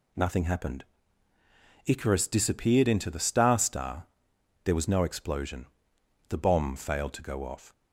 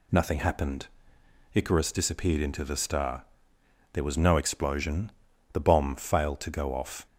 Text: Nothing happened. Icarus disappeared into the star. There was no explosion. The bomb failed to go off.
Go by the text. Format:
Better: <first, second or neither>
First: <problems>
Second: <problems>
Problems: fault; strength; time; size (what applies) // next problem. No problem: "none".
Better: second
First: says "star" twice; at 3.5 s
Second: none